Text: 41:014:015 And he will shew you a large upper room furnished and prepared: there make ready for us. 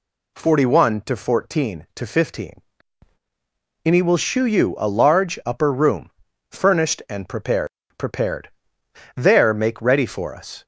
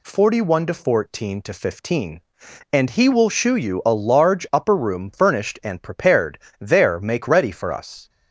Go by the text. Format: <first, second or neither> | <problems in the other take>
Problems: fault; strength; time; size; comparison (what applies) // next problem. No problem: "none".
second | pauses between "room" and "furnished"; at 6.0 s; 0.40 s long // says "prepared" twice; at 7.9 s